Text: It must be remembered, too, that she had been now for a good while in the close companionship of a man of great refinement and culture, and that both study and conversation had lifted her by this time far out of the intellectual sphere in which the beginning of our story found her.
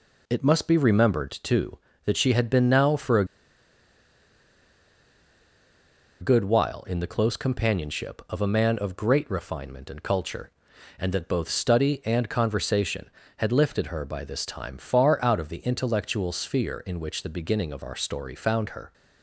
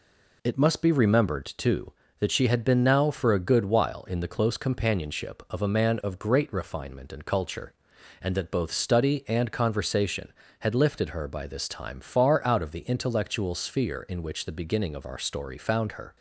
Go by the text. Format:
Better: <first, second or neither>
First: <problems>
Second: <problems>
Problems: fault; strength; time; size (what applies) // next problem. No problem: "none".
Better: second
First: pauses between "a" and "good"; strong; at 3.2 s; 2.9 s long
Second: none